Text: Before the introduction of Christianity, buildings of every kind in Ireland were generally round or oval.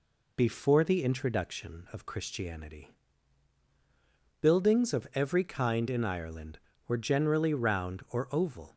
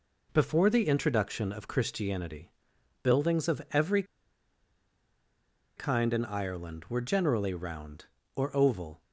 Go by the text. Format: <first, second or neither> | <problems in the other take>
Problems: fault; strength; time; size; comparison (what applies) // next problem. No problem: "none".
first | pauses between "every" and "kind"; strong; at 4.0 s; 1.7 s long